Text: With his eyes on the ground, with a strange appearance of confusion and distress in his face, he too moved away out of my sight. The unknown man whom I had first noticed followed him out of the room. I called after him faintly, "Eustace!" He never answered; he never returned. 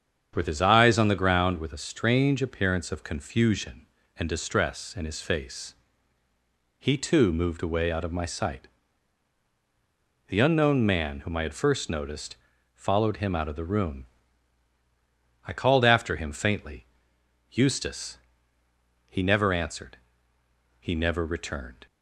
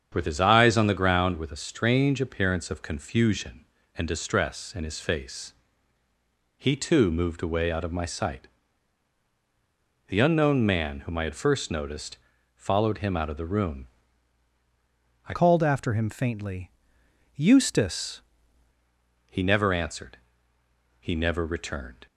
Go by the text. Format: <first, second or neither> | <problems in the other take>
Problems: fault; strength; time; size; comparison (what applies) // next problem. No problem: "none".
first | starts louder than the rest; strong; until 1.1 s; 7.5 dB; strong in the first // pauses between "noticed" and "followed"; at 12.1 s; 0.38 s long; also in the first // changes voice from "called" to "Eustace"; from 15.3 to 18.2 s; 2.9 s long